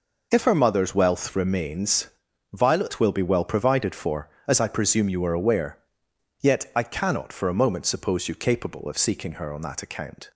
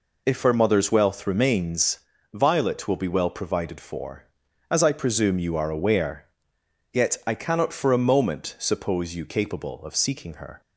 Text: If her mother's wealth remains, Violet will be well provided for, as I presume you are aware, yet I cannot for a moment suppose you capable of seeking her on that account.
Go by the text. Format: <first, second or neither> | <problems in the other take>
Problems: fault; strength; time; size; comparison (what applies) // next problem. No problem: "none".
first | stops before "on that account"; at 10.6 s